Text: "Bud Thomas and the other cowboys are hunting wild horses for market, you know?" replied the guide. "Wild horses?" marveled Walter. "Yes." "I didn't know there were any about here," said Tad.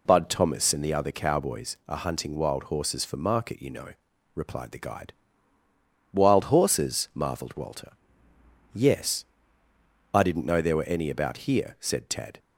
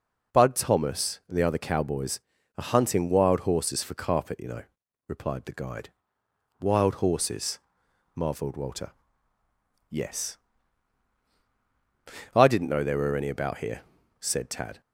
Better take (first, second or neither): first